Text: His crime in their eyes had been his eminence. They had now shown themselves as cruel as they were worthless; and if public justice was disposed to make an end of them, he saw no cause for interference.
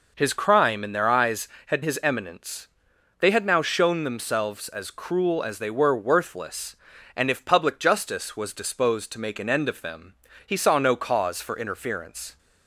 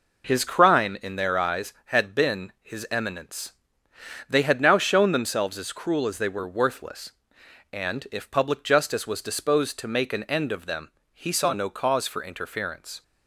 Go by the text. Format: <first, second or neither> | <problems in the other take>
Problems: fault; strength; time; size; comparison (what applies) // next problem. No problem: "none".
second | skips "been"; at 1.8 s